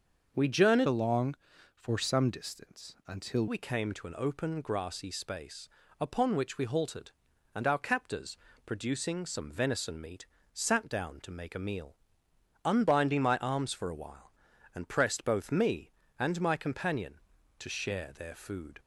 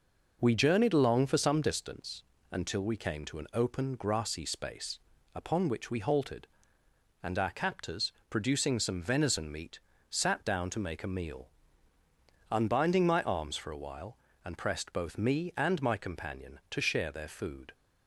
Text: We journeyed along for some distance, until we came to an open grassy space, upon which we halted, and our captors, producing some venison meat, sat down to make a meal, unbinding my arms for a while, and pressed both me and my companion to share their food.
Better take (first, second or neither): second